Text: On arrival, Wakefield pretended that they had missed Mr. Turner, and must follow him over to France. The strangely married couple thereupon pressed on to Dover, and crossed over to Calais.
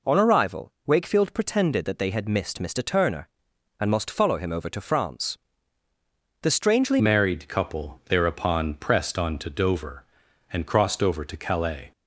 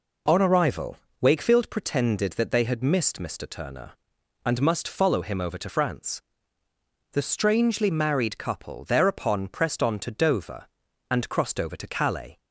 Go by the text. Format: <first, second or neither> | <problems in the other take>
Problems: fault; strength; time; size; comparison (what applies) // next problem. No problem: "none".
second | changes voice at "married"; from 6.9 s on; 5.0 s long